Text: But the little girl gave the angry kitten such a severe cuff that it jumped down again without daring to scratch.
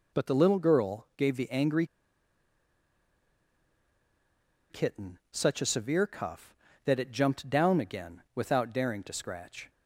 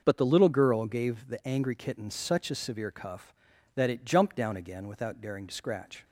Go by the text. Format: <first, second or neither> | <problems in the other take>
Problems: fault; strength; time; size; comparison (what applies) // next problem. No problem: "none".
second | pauses between "angry" and "kitten"; strong; at 1.8 s; 2.8 s long